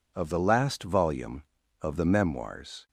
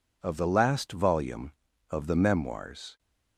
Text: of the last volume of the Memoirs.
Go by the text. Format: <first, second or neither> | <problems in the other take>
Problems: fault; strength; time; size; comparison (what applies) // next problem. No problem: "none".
neither | none